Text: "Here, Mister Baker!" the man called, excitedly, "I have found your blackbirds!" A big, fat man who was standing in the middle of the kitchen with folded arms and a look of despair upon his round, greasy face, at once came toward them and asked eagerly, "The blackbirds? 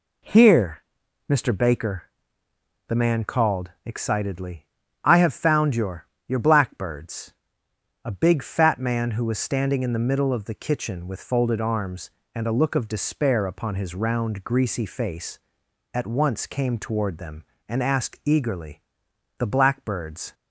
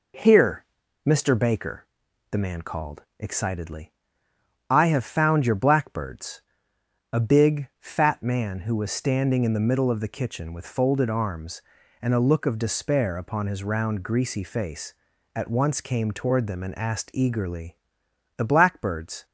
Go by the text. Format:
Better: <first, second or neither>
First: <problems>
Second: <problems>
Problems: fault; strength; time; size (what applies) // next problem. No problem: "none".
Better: second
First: says "your" twice; at 6.2 s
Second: none